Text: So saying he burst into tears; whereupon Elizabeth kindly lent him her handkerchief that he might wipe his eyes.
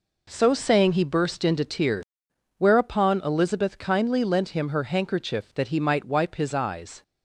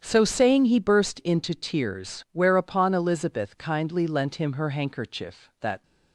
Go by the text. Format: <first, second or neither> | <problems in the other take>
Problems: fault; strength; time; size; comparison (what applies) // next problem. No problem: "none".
first | starts louder than the rest; strong; until 1.0 s; 9 dB // stops before "he might wipe his eyes"; at 5.8 s